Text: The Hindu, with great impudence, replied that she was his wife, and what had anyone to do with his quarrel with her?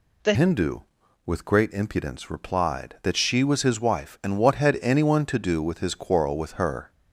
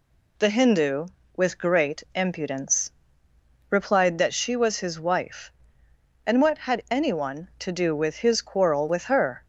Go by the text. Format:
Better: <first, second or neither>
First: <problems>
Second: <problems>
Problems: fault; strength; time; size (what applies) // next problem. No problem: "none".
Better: second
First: changes voice at "Hindu"; from 0.3 s on; 6.6 s long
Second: none